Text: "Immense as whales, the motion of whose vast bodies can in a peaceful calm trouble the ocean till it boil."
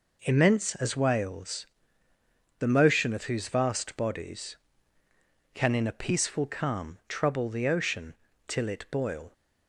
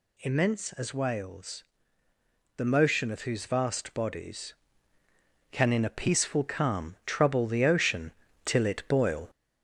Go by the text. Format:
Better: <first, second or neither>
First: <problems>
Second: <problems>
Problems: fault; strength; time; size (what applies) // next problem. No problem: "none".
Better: first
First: pauses between "ocean" and "till"; slight; at 8.1 s; 0.34 s long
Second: gets louder; noticeable; throughout; 4.5 dB // pauses between "ocean" and "till"; slight; at 8.0 s; 0.34 s long